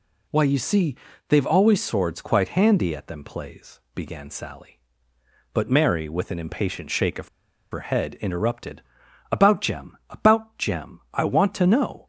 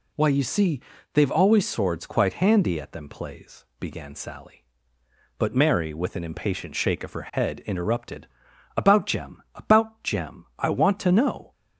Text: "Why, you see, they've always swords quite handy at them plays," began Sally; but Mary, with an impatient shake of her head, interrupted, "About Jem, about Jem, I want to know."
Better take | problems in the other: second | pauses between "of" and "her"; at 7.2 s; 0.43 s long

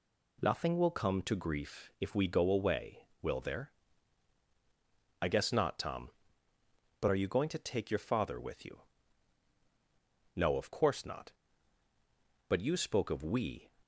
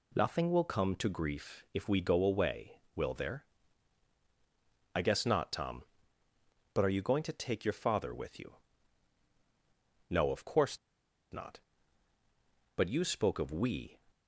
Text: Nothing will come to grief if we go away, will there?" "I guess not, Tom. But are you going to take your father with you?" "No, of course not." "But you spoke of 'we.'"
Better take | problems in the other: first | pauses between "course" and "not"; noticeable; at 10.7 s; 0.54 s long

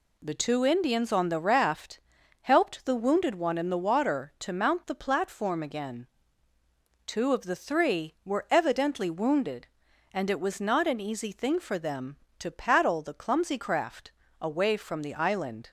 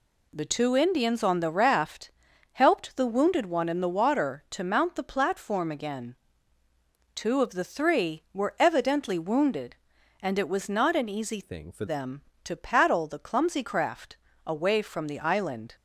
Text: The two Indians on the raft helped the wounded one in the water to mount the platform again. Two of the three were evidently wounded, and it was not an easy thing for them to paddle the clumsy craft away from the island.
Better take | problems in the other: first | pauses between "raft" and "helped"; at 2.1 s; 0.42 s long; also in the first // changes voice from "thing" to "for"; from 11.4 to 11.8 s; 0.4 s long // pauses between "craft" and "away"; slight; at 14.1 s; 0.30 s long; slight in the first

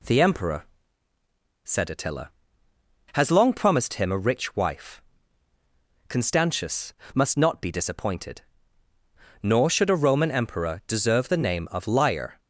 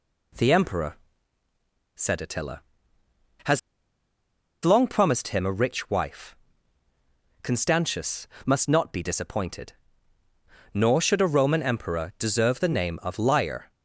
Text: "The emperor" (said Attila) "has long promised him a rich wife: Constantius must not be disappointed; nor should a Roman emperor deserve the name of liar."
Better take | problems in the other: first | pauses between "has" and "long"; at 3.5 s; 1.0 s long // pauses between "Constantius" and "must"; slight; at 8.2 s; 0.20 s long; slight in the first

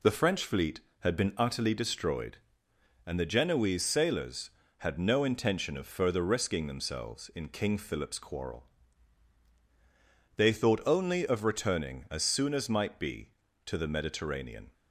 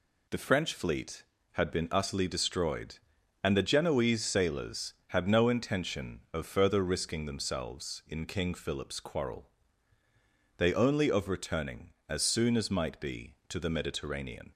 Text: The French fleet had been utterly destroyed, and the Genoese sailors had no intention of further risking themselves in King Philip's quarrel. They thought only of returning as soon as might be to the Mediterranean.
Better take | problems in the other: first | skips "thought"; at 10.7 s

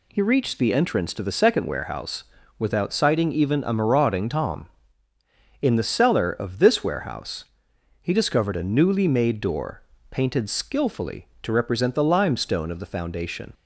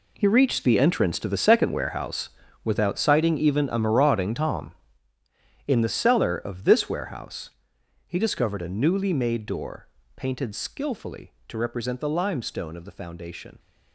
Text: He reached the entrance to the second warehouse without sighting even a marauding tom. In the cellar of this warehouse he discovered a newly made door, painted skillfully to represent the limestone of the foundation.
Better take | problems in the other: first | gets quieter; strong; throughout; 13.5 dB // pauses between "warehouse" and "without"; slight; at 2.2 s; 0.34 s long; slight in the first // pauses between "warehouse" and "he"; noticeable; at 7.4 s; 0.58 s long; noticeable in the first

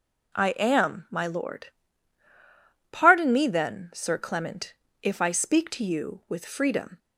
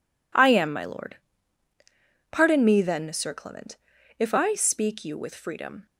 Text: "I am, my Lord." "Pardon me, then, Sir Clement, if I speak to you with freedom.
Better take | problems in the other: first | skips "to"; at 5.0 s

